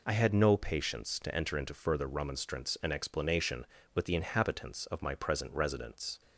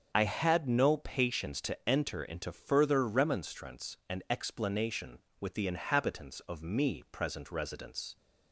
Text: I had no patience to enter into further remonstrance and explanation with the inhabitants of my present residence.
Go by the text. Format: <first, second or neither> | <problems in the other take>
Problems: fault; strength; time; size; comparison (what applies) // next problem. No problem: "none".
first | starts louder than the rest; until 1.1 s; 7 dB // says "me" for "my"; at 6.6 s